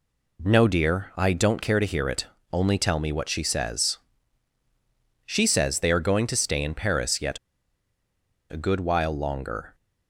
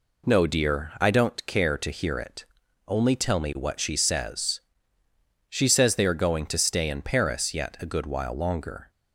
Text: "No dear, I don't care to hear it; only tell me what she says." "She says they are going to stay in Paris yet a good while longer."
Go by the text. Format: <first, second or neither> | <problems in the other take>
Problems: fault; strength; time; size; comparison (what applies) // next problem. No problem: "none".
second | pauses between "yet" and "a"; at 7.3 s; 1.1 s long